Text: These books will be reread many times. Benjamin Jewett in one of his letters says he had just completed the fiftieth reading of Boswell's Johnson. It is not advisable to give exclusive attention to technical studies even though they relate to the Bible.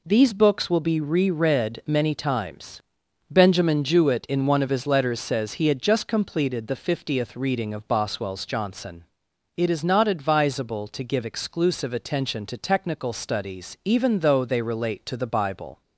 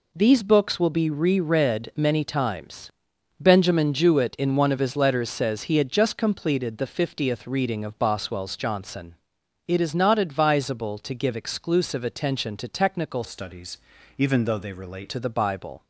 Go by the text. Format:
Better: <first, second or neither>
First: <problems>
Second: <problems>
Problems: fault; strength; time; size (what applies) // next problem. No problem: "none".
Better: first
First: none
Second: changes voice from "studies" to "relate"; from 13.2 to 15.0 s; 1.8 s long // pauses between "studies" and "even"; at 13.7 s; 0.40 s long